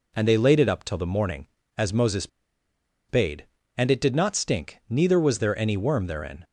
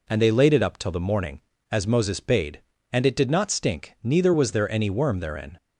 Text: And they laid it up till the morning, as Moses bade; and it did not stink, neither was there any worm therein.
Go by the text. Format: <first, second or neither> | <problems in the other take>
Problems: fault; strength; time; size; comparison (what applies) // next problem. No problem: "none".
second | pauses between "Moses" and "bade"; noticeable; at 2.2 s; 0.81 s long